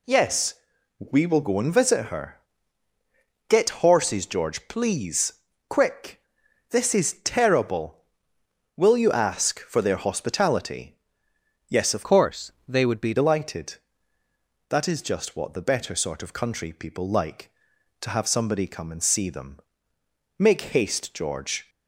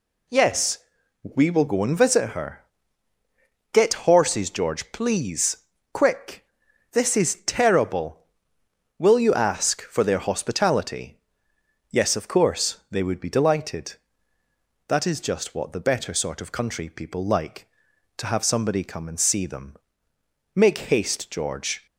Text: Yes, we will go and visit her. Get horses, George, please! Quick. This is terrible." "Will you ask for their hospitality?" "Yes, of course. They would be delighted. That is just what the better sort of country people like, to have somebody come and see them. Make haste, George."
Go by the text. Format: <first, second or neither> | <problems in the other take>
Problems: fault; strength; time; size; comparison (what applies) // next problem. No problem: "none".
second | changes voice from "course" to "be"; from 12.0 to 13.1 s; 1.1 s long // pauses between "Make" and "haste"; slight; at 20.6 s; 0.16 s long; slight in the second